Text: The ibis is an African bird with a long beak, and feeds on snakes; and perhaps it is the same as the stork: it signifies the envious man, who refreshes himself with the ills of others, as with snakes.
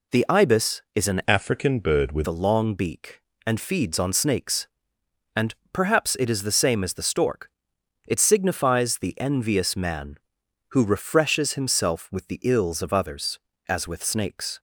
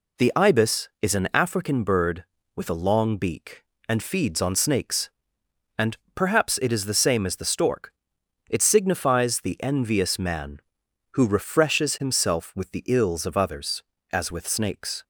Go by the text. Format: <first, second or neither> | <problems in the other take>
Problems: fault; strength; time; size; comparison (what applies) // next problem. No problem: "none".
second | changes voice from "African" to "with"; from 1.2 to 2.2 s; 1.0 s long // pauses between "and" and "perhaps"; slight; at 5.5 s; 0.16 s long; slight in the second